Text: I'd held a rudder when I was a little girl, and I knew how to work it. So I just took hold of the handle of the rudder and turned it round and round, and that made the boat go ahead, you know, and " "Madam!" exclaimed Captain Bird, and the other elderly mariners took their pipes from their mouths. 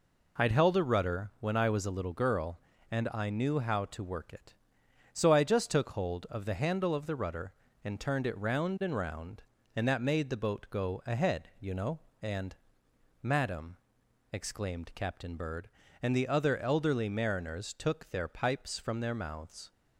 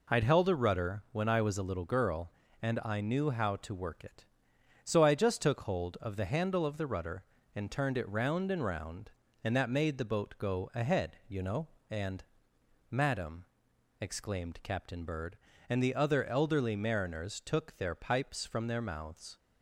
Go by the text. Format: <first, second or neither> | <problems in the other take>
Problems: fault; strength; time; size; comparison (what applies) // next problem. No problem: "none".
neither | none